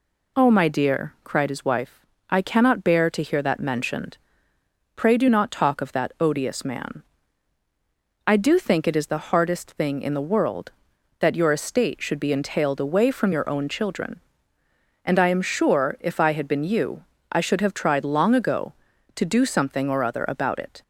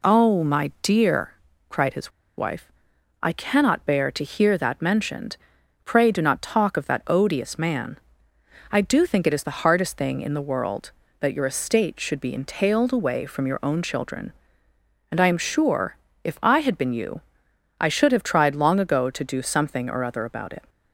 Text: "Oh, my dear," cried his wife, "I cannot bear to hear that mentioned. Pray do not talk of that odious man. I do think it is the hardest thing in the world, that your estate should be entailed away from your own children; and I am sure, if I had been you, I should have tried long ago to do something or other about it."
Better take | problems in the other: first | pauses between "his" and "wife"; slight; at 2.0 s; 0.27 s long

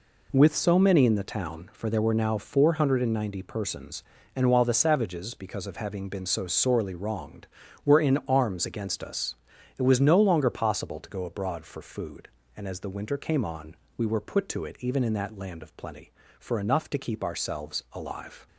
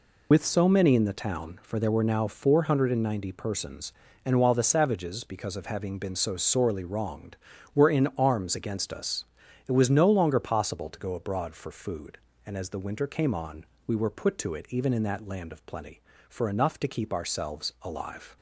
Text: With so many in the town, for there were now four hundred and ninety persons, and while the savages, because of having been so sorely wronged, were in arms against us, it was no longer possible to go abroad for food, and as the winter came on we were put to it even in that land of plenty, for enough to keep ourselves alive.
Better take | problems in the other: first | loses the start of "With"; at 0.3 s; 110 ms // pauses between "on" and "we"; slight; at 13.6 s; 0.22 s long; slight in the first

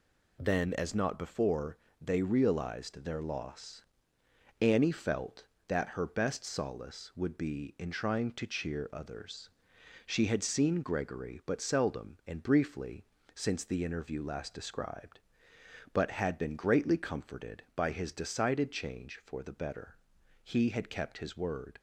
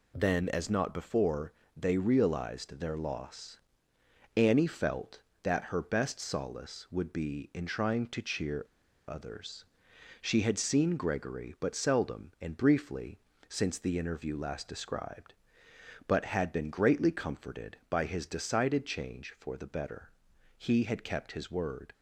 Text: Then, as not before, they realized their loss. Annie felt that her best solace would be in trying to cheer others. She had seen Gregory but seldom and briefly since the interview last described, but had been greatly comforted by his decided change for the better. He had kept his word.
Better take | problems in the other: first | pauses between "cheer" and "others"; at 8.6 s; 0.45 s long // pauses between "briefly" and "since"; slight; at 13.1 s; 0.30 s long; slight in the first

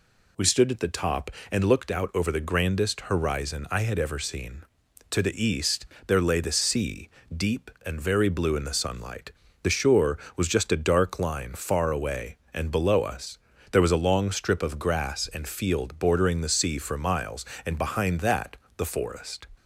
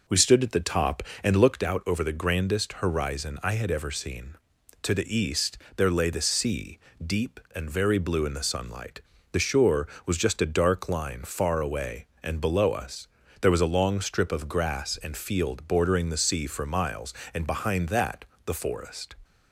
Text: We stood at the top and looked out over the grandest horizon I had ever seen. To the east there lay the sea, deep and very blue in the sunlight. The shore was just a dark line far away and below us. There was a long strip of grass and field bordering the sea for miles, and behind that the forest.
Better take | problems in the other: first | starts louder than the rest; noticeable; until 1.8 s; 5 dB // pauses between "east" and "there"; slight; at 5.5 s; 0.18 s long; slight in the first // pauses between "that" and "the"; slight; at 18.2 s; 0.20 s long; slight in the first

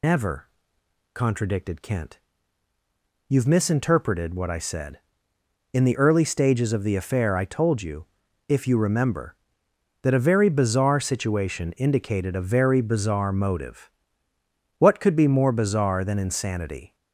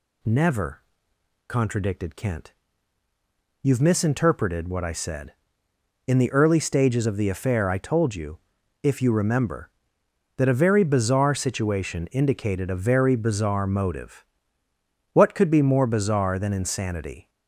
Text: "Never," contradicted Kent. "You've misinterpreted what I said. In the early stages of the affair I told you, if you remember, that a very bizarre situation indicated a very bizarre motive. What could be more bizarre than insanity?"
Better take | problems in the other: second | loses the start of "Never"; at 0.0 s; 140 ms

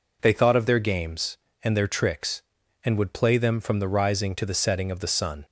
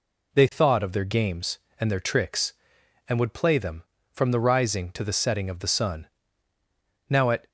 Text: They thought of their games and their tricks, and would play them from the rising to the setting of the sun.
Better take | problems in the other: first | goes on to say "Now at"; slight; from 7.0 s on; 0.40 s long

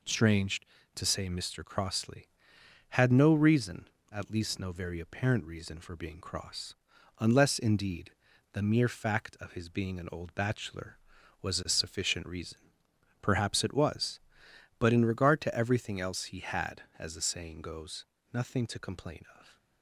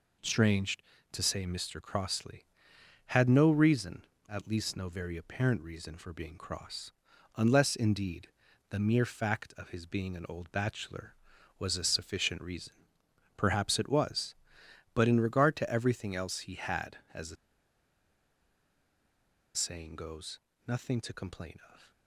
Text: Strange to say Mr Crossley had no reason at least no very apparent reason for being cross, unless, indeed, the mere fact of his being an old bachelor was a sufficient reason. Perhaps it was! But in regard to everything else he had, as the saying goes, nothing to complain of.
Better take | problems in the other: first | pauses between "the" and "saying"; strong; at 17.3 s; 2.1 s long

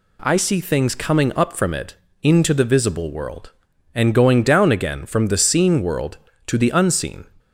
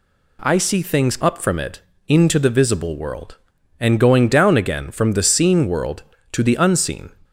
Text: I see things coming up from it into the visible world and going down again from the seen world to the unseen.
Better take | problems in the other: first | skips "coming"; at 1.1 s // pauses between "it" and "into"; slight; at 1.7 s; 0.28 s long; slight in the first

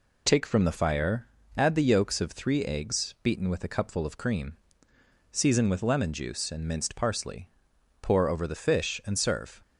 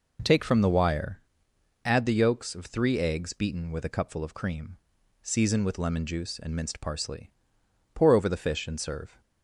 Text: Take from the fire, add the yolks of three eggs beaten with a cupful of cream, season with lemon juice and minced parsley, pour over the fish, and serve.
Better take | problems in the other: first | says "wire" for "fire"; at 0.6 s

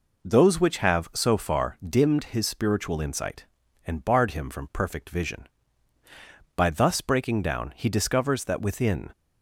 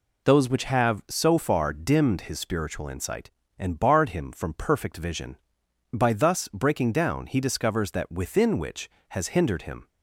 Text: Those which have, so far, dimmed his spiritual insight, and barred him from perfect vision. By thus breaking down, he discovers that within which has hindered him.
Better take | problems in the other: second | stops before "which has hindered him"; at 9.1 s

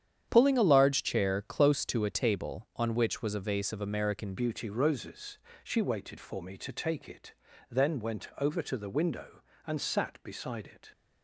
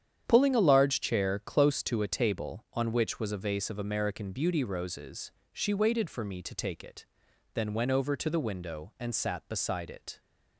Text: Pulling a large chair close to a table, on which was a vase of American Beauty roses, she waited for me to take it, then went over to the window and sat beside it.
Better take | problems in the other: second | starts louder than the rest; strong; until 1.2 s; 9 dB; strong in the second // changes voice at "Beauty"; from 4.3 s on; 6.6 s long

